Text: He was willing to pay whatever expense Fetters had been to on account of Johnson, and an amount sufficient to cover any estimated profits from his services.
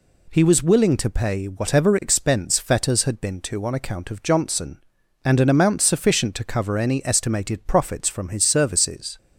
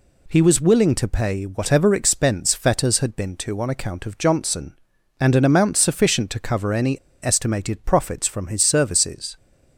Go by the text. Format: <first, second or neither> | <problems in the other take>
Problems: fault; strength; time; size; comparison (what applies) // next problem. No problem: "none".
first | pauses between "any" and "estimated"; slight; at 6.9 s; 0.25 s long